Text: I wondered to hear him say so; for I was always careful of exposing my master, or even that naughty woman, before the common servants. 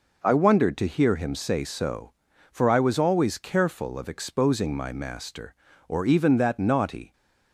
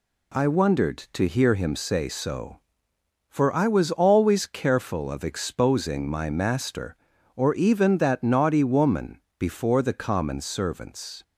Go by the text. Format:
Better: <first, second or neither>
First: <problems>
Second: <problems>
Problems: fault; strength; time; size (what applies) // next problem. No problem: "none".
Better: second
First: stops before "woman before the common servants"; at 7.1 s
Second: none